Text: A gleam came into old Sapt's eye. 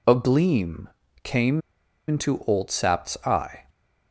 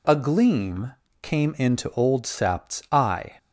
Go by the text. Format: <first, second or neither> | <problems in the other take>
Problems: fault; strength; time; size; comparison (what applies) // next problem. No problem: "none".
second | pauses between "gleam" and "came"; slight; at 0.8 s; 0.34 s long; slight in the second // pauses between "came" and "into"; noticeable; at 1.6 s; 0.47 s long